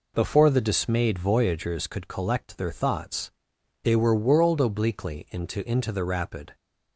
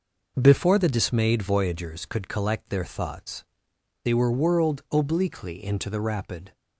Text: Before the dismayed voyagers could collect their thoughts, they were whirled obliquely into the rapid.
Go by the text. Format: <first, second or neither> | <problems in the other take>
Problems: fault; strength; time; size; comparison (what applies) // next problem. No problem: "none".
second | says "into" twice; at 5.6 s